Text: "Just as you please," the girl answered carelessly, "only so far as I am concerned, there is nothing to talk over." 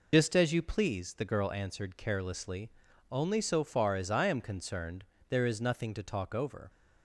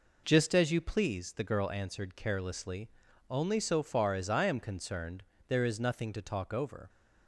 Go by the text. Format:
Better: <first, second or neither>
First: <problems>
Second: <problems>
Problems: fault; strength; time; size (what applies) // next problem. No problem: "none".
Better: second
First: loses the start of "Just"; at 0.1 s; 70 ms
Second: none